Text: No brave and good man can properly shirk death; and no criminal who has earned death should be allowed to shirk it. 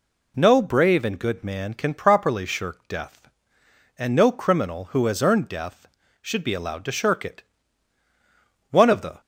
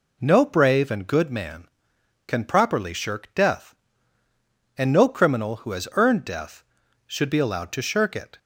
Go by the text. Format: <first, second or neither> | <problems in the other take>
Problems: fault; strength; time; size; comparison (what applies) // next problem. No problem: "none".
second | goes on to say "One of the"; from 8.7 s on; 0.50 s long